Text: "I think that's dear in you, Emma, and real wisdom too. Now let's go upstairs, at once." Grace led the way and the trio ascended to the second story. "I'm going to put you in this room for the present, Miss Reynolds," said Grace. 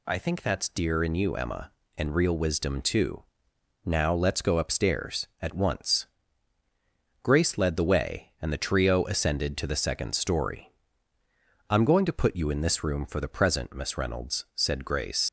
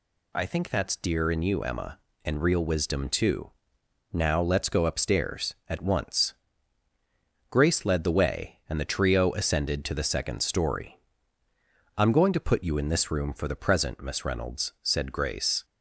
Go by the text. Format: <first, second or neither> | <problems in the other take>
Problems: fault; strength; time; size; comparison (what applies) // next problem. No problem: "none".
second | leaves "Grace" unfinished; at 15.2 s; 85 ms